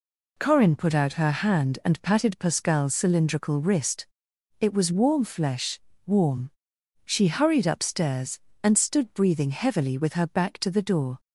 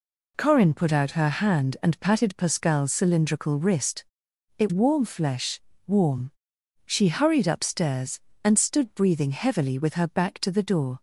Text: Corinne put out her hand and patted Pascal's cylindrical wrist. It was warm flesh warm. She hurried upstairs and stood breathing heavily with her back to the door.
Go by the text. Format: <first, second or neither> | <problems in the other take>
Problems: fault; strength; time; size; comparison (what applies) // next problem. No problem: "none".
first | skips "was"; at 4.7 s // pauses between "flesh" and "warm"; slight; at 5.6 s; 0.26 s long; slight in the first